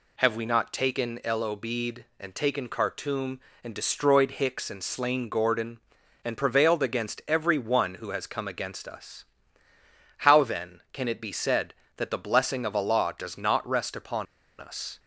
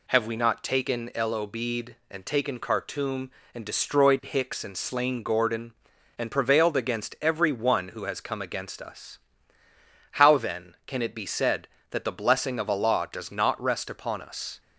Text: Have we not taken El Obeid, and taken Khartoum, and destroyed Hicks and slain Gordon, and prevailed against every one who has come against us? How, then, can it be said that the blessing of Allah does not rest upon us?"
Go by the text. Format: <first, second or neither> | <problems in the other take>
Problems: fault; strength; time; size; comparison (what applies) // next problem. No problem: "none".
second | pauses between "upon" and "us"; slight; at 14.2 s; 0.33 s long